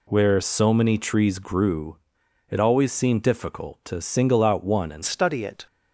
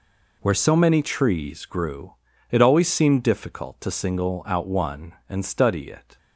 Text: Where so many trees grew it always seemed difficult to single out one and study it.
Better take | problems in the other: second | pauses between "grew" and "it"; noticeable; at 1.9 s; 0.50 s long; also in the second // changes voice at "study"; from 5.0 s on; 0.6 s long

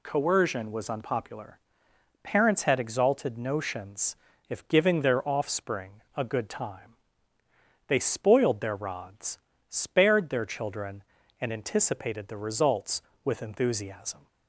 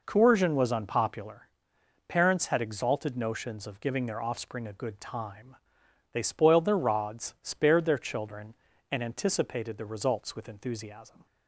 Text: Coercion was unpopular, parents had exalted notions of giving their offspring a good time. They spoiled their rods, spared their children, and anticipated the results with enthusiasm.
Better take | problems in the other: second | says "if" for "of"; at 4.4 s // pauses between "offspring" and "a"; slight; at 6.0 s; 0.16 s long

